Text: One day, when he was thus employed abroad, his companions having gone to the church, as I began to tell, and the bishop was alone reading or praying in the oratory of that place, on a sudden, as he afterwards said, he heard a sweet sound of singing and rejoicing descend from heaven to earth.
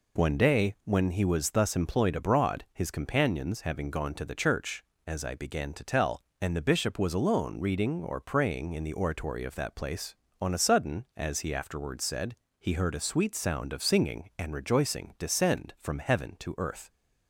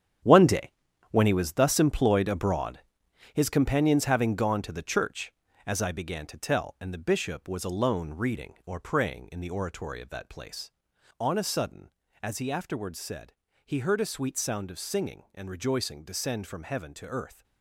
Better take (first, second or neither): first